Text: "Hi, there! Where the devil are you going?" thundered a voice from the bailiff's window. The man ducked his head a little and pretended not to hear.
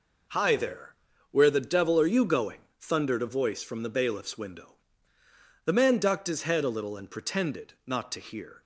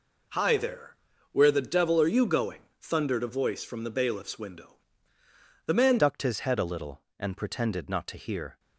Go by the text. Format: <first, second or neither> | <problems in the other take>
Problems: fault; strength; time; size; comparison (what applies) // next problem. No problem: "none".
first | changes voice at "ducked"; from 5.9 s on; 2.6 s long